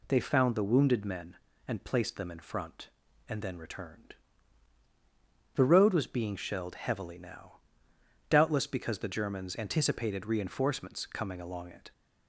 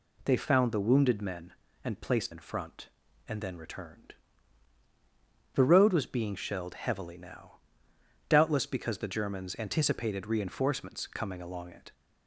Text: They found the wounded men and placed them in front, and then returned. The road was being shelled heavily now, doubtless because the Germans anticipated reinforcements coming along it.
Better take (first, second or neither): first